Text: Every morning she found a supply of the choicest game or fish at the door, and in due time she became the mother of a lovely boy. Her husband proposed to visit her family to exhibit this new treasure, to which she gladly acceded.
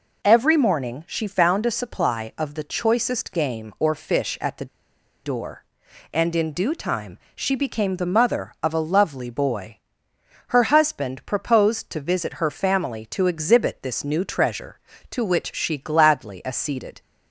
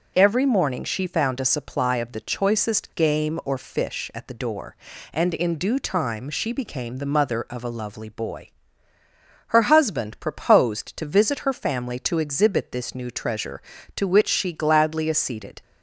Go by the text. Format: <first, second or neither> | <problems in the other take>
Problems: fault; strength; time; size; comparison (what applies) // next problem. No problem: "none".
second | pauses between "the" and "door"; noticeable; at 4.6 s; 0.57 s long // pauses between "time" and "she"; slight; at 7.1 s; 0.18 s long